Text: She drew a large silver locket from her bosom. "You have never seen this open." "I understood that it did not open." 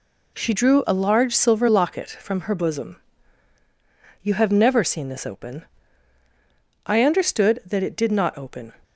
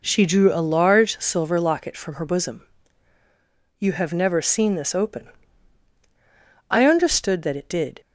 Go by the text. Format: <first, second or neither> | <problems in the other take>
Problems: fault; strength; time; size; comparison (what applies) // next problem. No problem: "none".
first | stops before "not open"; at 8.0 s